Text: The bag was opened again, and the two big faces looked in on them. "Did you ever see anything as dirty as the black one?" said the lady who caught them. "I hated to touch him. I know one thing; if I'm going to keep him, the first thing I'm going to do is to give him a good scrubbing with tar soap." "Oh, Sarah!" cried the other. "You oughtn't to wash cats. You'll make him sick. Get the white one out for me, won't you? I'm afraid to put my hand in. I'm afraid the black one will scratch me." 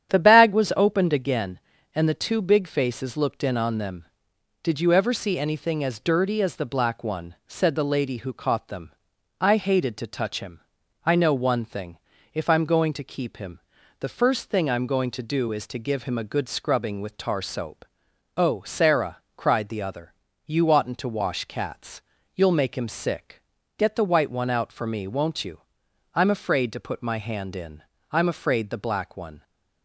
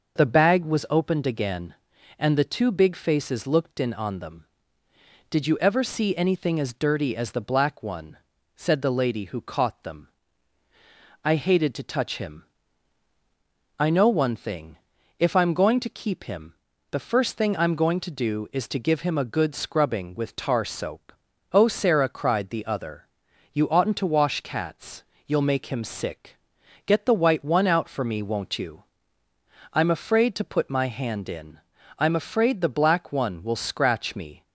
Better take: second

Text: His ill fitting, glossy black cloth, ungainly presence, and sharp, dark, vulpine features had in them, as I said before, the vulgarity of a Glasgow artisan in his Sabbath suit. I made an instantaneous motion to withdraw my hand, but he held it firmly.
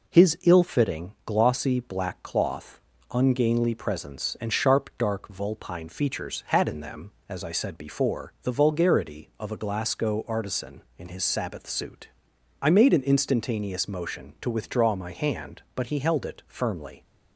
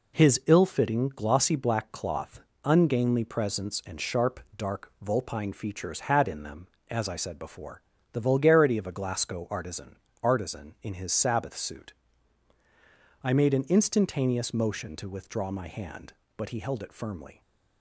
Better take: first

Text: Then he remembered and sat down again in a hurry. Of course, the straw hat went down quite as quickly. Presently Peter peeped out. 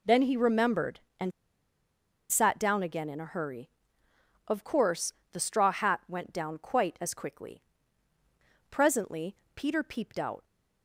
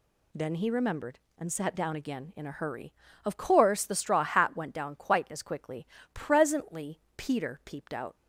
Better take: second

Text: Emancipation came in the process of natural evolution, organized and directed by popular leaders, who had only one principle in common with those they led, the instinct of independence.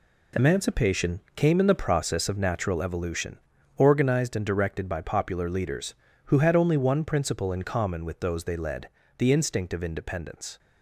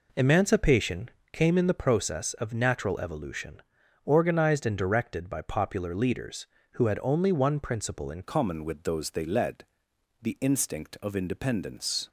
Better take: first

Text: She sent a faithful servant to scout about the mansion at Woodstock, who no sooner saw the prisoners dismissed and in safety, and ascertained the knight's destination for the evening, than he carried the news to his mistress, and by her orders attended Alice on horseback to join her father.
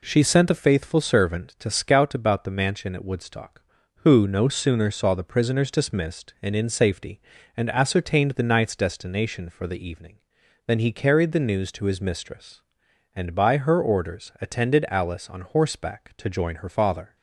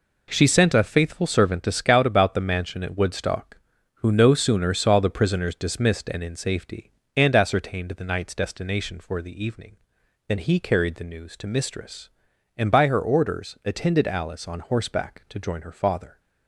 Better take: first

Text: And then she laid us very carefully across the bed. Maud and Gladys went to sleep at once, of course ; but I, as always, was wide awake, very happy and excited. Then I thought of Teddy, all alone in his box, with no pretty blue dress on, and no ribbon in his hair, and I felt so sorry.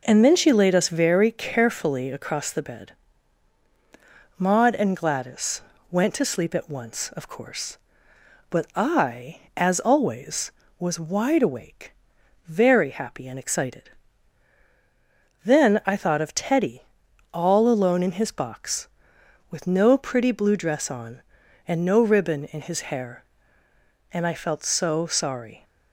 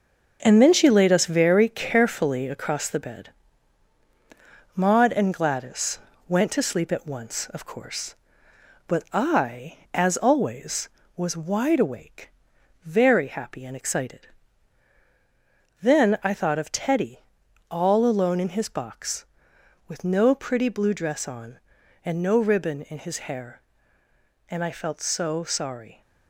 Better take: first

